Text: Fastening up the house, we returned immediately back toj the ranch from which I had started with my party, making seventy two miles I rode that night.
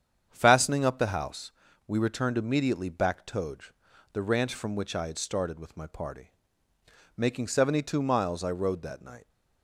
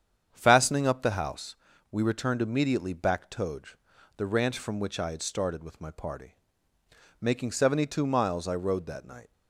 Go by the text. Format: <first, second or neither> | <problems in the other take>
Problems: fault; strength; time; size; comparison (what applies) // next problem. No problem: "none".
neither | starts louder than the rest; strong; the same in both // pauses between "toj" and "the"; the same in both